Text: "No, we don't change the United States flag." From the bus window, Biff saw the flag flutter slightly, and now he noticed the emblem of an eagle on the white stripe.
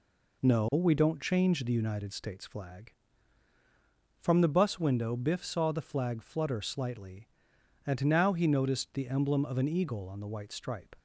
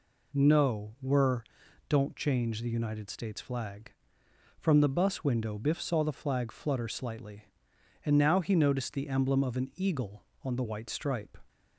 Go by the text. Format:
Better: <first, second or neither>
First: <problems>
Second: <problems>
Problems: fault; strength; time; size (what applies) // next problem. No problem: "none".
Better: first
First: none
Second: says "were" for "we"; at 1.0 s